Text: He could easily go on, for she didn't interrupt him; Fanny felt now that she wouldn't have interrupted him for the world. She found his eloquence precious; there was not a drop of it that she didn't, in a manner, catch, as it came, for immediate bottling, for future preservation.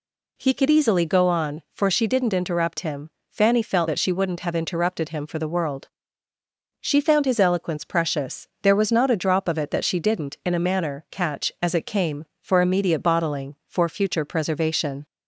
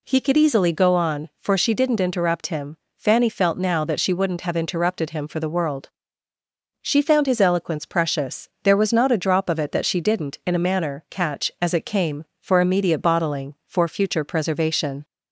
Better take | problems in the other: second | skips "now"; at 3.8 s

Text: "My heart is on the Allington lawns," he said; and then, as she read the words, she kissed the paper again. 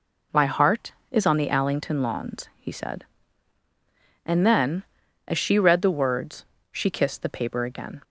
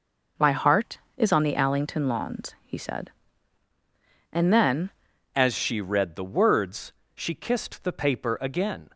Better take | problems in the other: first | changes voice at "as"; from 5.3 s on; 3.5 s long

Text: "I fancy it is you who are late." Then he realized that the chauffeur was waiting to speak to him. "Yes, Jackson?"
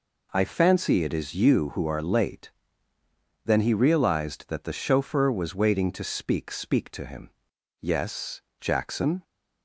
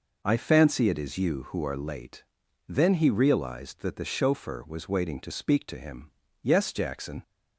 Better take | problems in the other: second | says "speak" twice; at 6.5 s

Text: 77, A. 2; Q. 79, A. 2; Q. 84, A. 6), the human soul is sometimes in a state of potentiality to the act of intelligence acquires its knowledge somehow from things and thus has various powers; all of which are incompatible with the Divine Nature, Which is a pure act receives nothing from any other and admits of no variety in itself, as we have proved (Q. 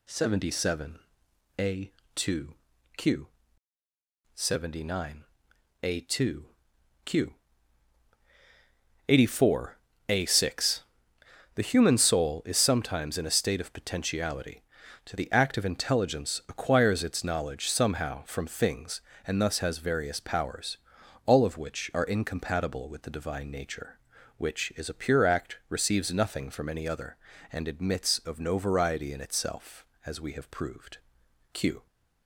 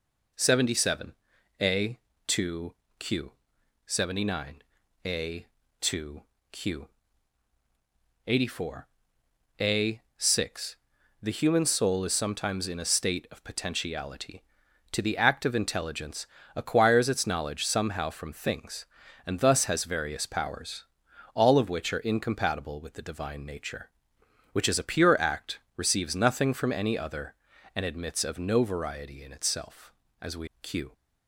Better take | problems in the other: first | pauses between "intelligence" and "acquires"; slight; at 16.2 s; 0.28 s long // pauses between "act" and "receives"; slight; at 25.5 s; 0.18 s long // skips "have proved"; at 30.5 s

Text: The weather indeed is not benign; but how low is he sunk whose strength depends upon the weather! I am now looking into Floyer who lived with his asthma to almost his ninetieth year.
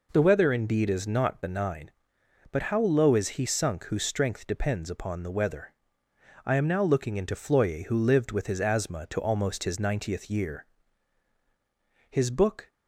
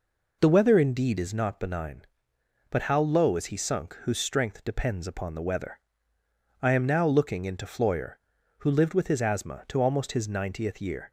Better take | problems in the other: second | goes on to say "His book"; noticeable; from 12.0 s on; 0.62 s long

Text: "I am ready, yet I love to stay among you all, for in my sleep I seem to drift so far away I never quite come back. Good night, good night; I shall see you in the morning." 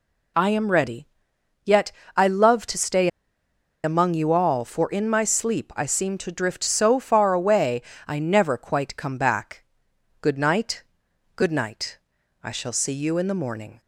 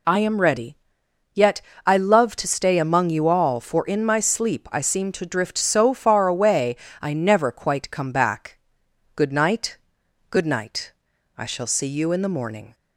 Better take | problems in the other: second | pauses between "yet" and "I"; slight; at 1.9 s; 0.24 s long; slight in the second // pauses between "stay" and "among"; noticeable; at 3.0 s; 0.75 s long // pauses between "away" and "I"; slight; at 7.8 s; 0.26 s long; slight in the second

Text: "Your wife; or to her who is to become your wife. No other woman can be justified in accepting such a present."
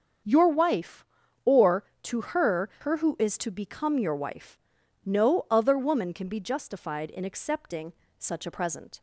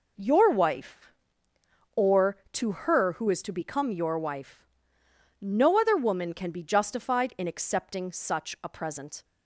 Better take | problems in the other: second | starts louder than the rest; until 1.6 s; 7 dB // says "her" twice; at 2.8 s // pauses between "accepting" and "such"; slight; at 7.9 s; 0.28 s long

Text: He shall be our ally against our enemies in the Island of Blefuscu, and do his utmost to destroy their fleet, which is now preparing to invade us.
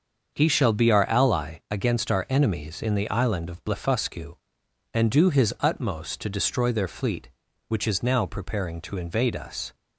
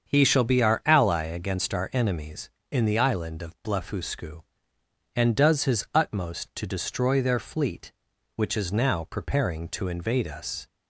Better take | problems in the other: first | starts louder than the rest; until 1.1 s; 7 dB; also in the first // says "does" for "do"; at 5.3 s

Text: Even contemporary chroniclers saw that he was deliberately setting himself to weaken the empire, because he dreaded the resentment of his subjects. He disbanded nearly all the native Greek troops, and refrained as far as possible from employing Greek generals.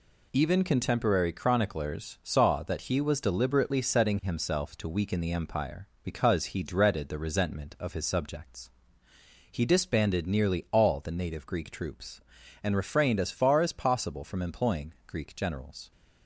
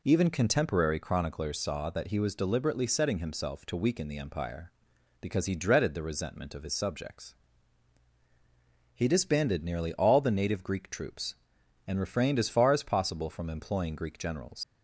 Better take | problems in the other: first | leaves "generals" unfinished; at 14.6 s; 95 ms

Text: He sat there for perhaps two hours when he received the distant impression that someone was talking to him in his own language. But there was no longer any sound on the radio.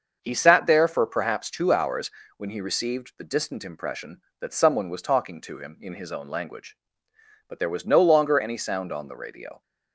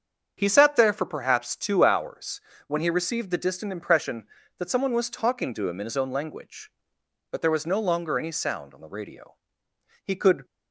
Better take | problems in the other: first | starts louder than the rest; until 1.3 s; 7 dB; also in the first // pauses between "hours" and "when"; slight; at 2.3 s; 0.30 s long; slight in the first // goes on to say "He could"; slight; from 10.0 s on; 0.40 s long

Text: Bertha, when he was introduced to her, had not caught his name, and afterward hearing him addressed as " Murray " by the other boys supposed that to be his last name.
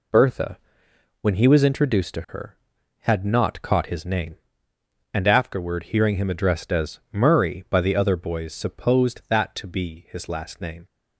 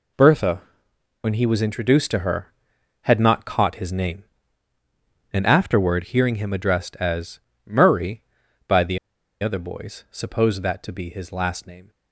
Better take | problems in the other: first | pauses between "the" and "other"; at 8.9 s; 0.43 s long

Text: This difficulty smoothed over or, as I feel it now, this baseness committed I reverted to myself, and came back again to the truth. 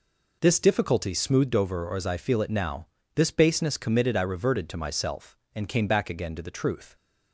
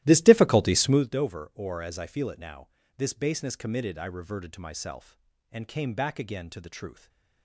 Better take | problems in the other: first | starts louder than the rest; strong; until 1.0 s; 15 dB // stays silent after the last word; slight; from 6.9 s on; 0.5 s long

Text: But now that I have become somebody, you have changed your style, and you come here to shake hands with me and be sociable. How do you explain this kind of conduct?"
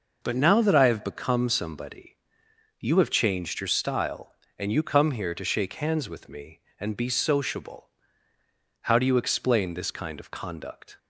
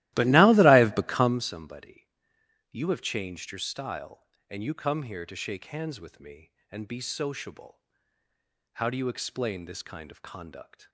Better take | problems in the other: first | starts louder than the rest; strong; until 1.4 s; 16 dB

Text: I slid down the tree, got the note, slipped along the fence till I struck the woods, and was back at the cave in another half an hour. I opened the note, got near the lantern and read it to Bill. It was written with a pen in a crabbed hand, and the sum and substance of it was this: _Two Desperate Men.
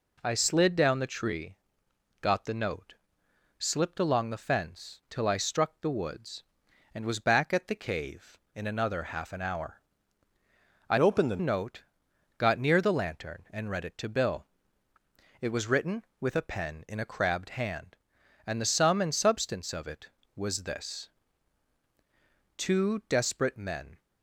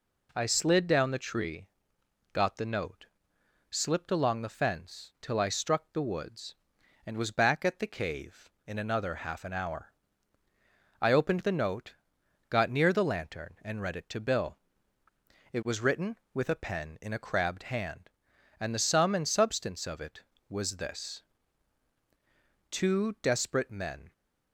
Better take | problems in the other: second | changes voice from "opened" to "the"; from 10.9 to 11.3 s; 0.4 s long

